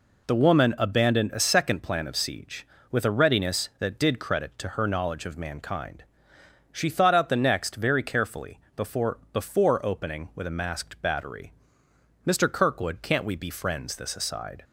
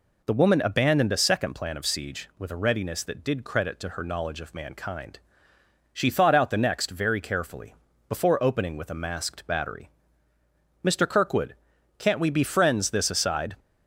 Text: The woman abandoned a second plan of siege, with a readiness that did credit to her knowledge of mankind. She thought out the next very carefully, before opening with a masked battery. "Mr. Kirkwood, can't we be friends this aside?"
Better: second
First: says "before" twice; at 9.3 s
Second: none

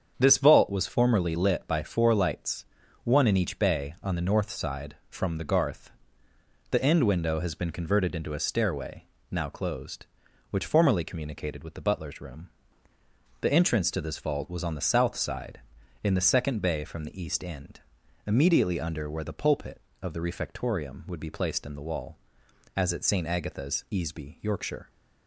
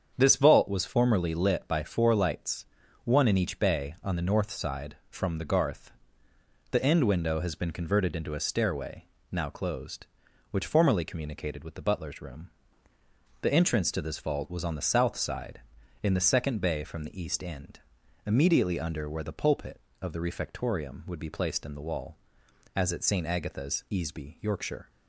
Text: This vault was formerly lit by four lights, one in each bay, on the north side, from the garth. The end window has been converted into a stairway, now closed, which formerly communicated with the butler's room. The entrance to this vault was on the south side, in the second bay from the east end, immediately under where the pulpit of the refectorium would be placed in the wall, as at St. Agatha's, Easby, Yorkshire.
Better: neither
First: starts louder than the rest; strong; until 1.1 s; 7.5 dB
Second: starts louder than the rest; strong; until 1.1 s; 7.5 dB

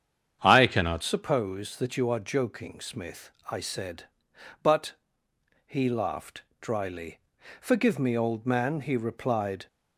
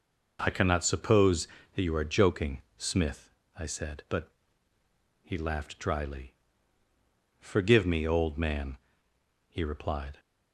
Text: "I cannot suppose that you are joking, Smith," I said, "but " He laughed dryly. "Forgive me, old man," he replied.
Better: second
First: starts louder than the rest; strong; until 1.4 s; 8.5 dB // changes voice at "suppose"; from 1.0 s on; 8.6 s long // pauses between "laughed" and "dryly"; slight; at 6.4 s; 0.18 s long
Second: none

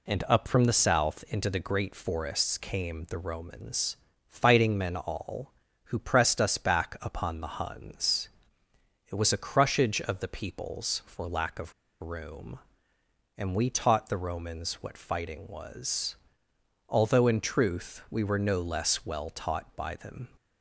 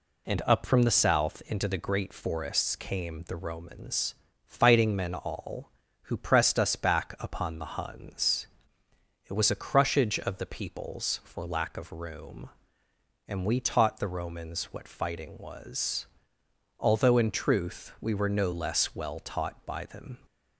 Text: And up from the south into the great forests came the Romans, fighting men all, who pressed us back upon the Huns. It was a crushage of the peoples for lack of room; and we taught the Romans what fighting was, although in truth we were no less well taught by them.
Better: second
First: pauses between "of" and "room"; slight; at 11.7 s; 0.28 s long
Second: none

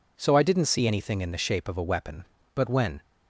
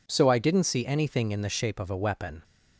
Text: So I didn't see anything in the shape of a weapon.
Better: second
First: goes on to say "But when"; slight; from 2.5 s on; 0.48 s long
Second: none

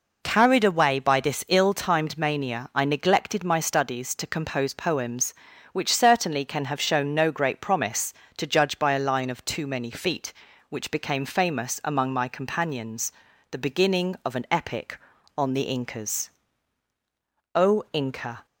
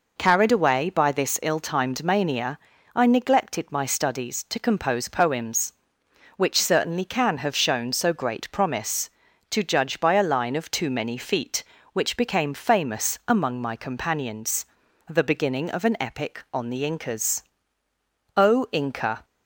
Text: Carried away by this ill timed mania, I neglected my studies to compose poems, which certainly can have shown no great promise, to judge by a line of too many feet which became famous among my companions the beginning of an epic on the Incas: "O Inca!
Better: first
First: pauses between "companions" and "the"; at 13.1 s; 0.38 s long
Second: says "so" for "no"; at 7.9 s // pauses between "companions" and "the"; at 14.6 s; 0.42 s long

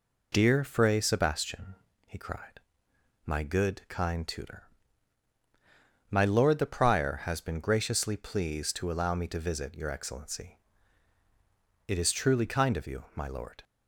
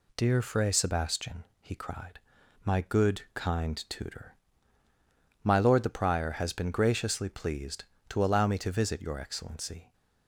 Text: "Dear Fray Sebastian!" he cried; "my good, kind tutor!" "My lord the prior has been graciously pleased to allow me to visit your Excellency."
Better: second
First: goes on to say "It is truly kind of you my lord"; strong; from 11.8 s on; 1.7 s long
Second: none

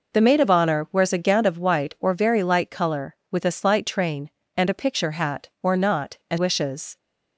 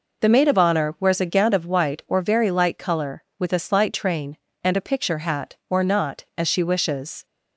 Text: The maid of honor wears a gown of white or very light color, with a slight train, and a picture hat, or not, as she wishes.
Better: second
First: skips "she"; at 6.3 s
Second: none

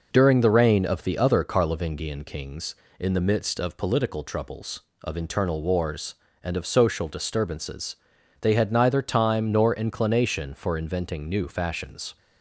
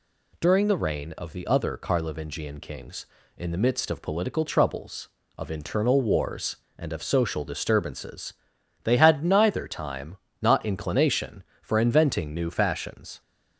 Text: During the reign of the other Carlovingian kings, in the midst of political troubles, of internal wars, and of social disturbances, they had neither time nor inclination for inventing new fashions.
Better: first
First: none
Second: says "not" for "nor"; at 10.4 s

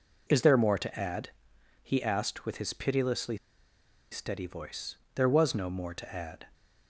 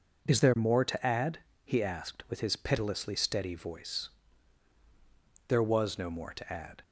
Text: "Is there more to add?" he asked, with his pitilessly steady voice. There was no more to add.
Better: second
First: pauses between "pitilessly" and "steady"; noticeable; at 3.3 s; 0.74 s long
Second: none

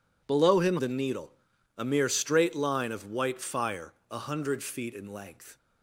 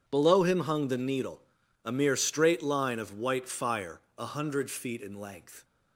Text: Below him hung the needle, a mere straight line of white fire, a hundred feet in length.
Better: second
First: skips "hung"; at 0.7 s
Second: none

